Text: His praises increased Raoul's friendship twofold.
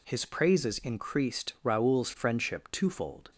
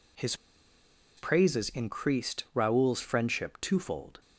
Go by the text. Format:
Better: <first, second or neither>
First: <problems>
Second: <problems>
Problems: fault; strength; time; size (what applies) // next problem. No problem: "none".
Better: first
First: none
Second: pauses between "His" and "praises"; noticeable; at 0.3 s; 0.82 s long